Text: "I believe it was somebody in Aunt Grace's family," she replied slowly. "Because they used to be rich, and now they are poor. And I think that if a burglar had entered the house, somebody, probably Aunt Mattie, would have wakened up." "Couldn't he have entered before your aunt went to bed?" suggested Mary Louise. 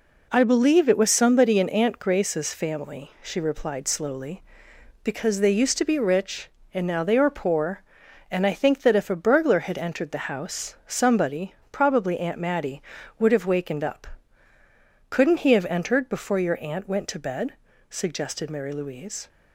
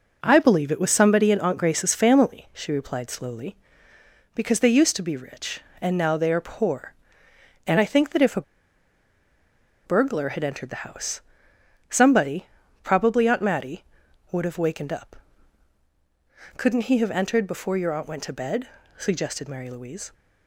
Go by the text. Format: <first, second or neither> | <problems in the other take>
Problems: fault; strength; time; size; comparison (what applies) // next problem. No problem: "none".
first | pauses between "a" and "burglar"; strong; at 8.4 s; 1.4 s long